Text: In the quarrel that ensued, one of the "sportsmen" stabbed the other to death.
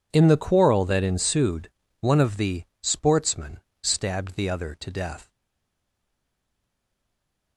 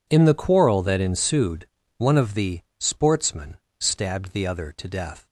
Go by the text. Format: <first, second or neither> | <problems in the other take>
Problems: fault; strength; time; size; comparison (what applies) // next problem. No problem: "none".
second | pauses between "the" and "sportsmen"; slight; at 2.6 s; 0.18 s long; slight in the second // pauses between "sportsmen" and "stabbed"; slight; at 3.6 s; 0.20 s long; slight in the second // stays silent after the last word; from 5.3 s on; 2.2 s long